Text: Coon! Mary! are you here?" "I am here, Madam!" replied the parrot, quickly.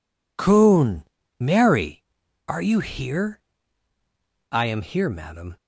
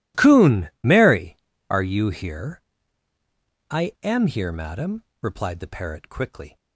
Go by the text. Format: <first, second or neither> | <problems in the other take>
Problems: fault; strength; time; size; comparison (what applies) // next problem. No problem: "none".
second | stops before "replied the parrot quickly"; at 5.5 s